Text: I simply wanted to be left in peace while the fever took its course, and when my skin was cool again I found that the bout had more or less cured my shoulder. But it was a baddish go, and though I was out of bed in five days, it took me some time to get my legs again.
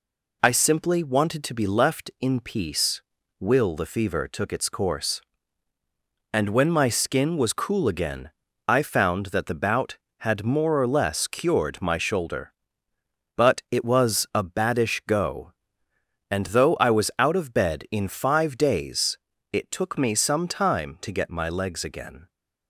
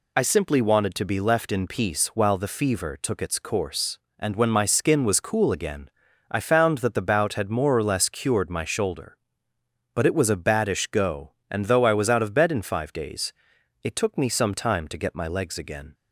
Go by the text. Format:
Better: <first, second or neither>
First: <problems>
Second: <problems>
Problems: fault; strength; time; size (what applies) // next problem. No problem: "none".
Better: second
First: says "will" for "while"; at 3.3 s // pauses between "again" and "I"; slight; at 8.2 s; 0.36 s long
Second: pauses between "again" and "I"; at 5.8 s; 0.44 s long